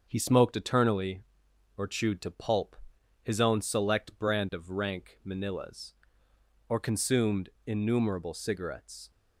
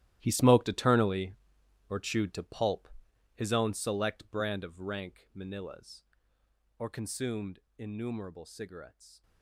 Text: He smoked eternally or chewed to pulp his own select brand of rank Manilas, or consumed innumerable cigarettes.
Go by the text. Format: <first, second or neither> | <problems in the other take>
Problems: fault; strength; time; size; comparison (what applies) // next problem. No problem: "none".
first | gets quieter; strong; throughout; 14.5 dB // starts louder than the rest; strong; until 1.2 s; 14 dB; also in the first // pauses between "pulp" and "his"; noticeable; at 2.8 s; 0.46 s long; noticeable in the first // pauses between "consumed" and "innumerable"; slight; at 7.5 s; 0.17 s long; slight in the first